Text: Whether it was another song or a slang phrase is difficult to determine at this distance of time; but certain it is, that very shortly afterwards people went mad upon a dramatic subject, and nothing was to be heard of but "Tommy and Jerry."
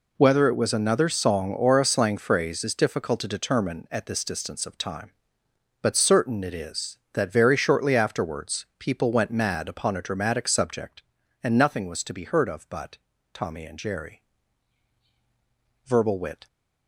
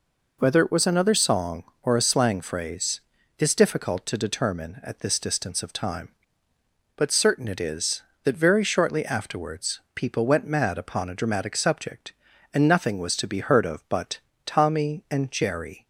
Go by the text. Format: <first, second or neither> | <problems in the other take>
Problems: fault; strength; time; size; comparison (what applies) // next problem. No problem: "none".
second | pauses between "but" and "Tommy"; at 12.9 s; 0.38 s long; slight in the second // goes on to say "Verbal wit"; noticeable; from 15.8 s on; 0.62 s long